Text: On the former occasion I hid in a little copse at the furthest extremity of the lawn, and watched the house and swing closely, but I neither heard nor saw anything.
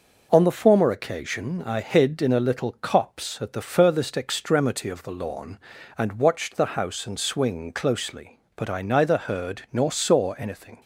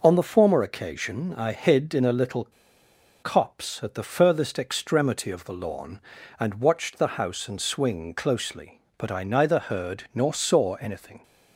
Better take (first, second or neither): first